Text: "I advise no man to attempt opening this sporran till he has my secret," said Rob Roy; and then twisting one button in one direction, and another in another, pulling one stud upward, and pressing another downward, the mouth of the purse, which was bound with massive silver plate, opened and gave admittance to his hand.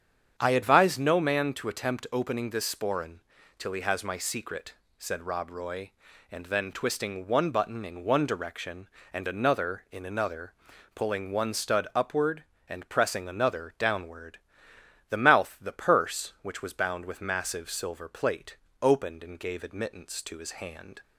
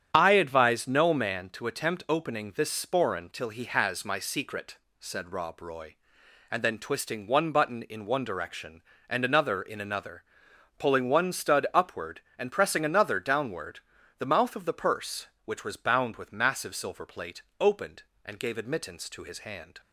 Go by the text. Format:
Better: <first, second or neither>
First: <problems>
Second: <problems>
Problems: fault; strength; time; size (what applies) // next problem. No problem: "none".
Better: second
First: starts louder than the rest; strong; until 1.3 s; 8 dB // pauses between "sporran" and "till"; slight; at 3.2 s; 0.36 s long // skips "of"; at 15.5 s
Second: starts louder than the rest; strong; until 1.1 s; 9.5 dB